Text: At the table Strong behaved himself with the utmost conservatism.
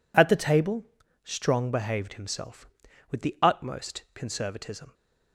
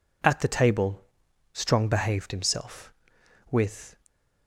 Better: first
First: pauses between "table" and "Strong"; at 0.8 s; 0.40 s long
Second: pauses between "table" and "Strong"; noticeable; at 1.0 s; 0.52 s long // stops before "the utmost conservatism"; at 4.0 s

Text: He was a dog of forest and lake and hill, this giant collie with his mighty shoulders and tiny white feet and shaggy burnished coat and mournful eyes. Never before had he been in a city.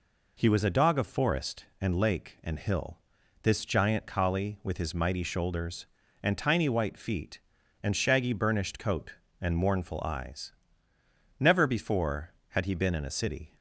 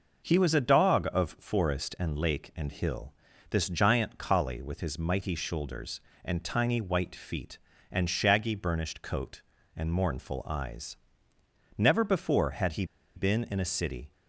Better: first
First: none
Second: pauses between "he" and "been"; slight; at 12.8 s; 0.31 s long

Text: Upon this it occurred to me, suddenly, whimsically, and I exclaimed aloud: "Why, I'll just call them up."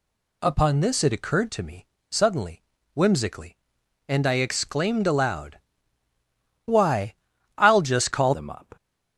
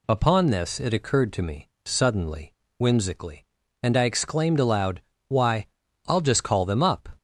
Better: second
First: changes voice at "them"; from 8.3 s on; 0.4 s long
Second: none

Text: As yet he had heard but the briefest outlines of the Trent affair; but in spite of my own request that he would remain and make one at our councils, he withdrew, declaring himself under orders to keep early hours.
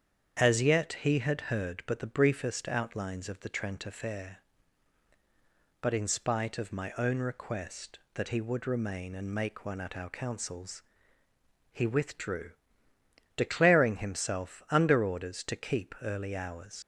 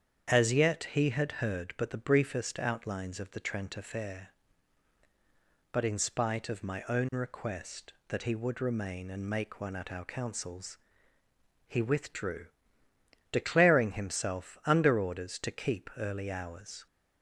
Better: second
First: starts louder than the rest; strong; until 1.4 s; 8 dB // leaves "hours" unfinished; at 16.8 s; 85 ms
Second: starts louder than the rest; strong; until 1.3 s; 8 dB

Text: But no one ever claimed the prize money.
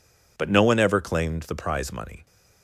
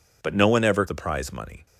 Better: first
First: none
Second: skips "claimed"; at 0.8 s

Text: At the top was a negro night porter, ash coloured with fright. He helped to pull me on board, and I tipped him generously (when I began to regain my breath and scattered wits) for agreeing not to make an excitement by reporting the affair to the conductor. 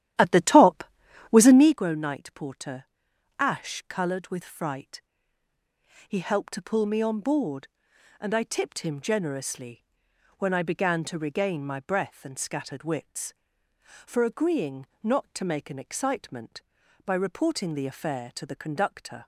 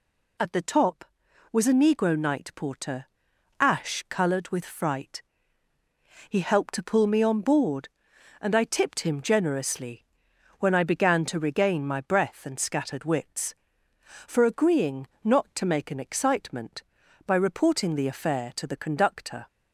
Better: second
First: starts louder than the rest; strong; until 1.8 s; 12 dB // pauses between "agreeing" and "not"; slight; at 14.8 s; 0.18 s long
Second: pauses between "agreeing" and "not"; slight; at 15.0 s; 0.18 s long

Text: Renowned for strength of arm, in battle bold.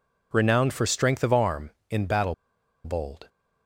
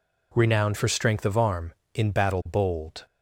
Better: second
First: pauses between "battle" and "bold"; noticeable; at 2.3 s; 0.51 s long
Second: none

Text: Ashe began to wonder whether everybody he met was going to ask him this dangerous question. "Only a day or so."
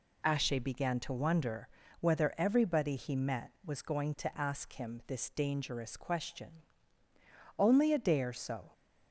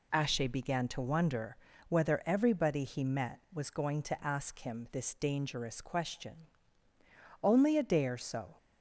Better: neither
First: pauses between "wonder" and "whether"; slight; at 1.6 s; 0.34 s long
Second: pauses between "wonder" and "whether"; slight; at 1.5 s; 0.34 s long

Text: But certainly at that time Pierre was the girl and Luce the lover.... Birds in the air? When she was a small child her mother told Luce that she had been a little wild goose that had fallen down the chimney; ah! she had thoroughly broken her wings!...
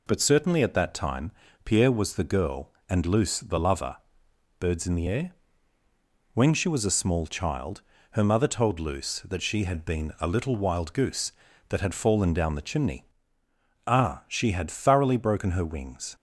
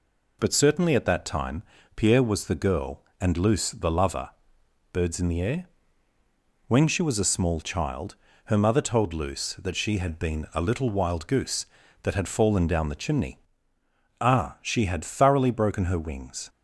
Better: neither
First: pauses between "time" and "Pierre"; slight; at 1.3 s; 0.34 s long // pauses between "child" and "her"; slight; at 7.8 s; 0.30 s long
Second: pauses between "time" and "Pierre"; slight; at 1.6 s; 0.34 s long // pauses between "child" and "her"; slight; at 8.1 s; 0.30 s long

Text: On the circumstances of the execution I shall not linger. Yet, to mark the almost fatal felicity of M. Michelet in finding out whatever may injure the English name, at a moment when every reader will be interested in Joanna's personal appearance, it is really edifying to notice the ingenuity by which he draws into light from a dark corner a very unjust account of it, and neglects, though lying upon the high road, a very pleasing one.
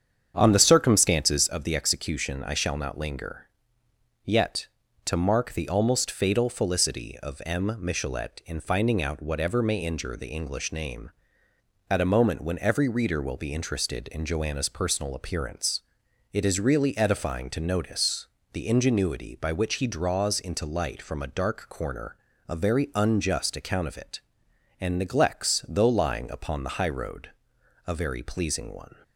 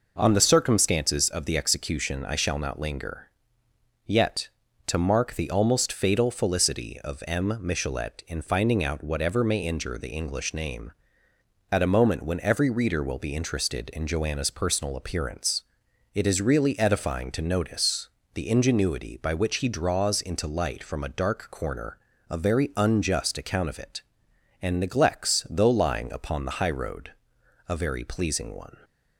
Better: second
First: starts louder than the rest; strong; until 1.7 s; 8 dB // pauses between "notice" and "the"; slight; at 18.2 s; 0.24 s long // pauses between "corner" and "a"; slight; at 22.1 s; 0.32 s long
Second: pauses between "notice" and "the"; slight; at 18.0 s; 0.24 s long // pauses between "corner" and "a"; slight; at 21.9 s; 0.32 s long

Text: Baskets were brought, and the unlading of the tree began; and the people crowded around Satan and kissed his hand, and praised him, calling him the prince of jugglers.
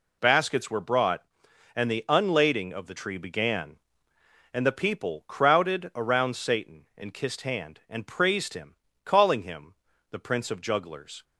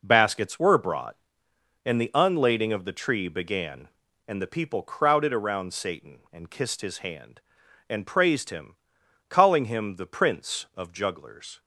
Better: second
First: skips "his"; at 7.4 s // pauses between "him" and "the"; at 9.7 s; 0.38 s long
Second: none

